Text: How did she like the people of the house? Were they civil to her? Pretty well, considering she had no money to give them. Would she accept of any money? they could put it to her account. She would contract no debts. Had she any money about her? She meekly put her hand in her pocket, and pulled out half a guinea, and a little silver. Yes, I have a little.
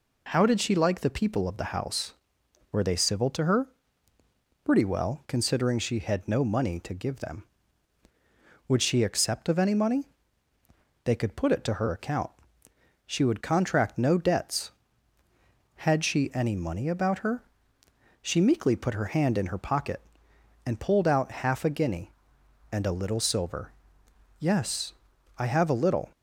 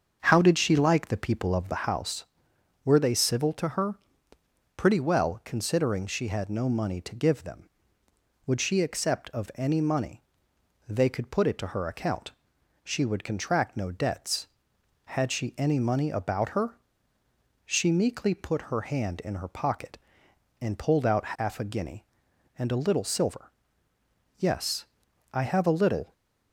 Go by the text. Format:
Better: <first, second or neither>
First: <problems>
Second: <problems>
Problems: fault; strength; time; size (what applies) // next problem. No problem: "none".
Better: first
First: none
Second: starts louder than the rest; until 1.9 s; 7 dB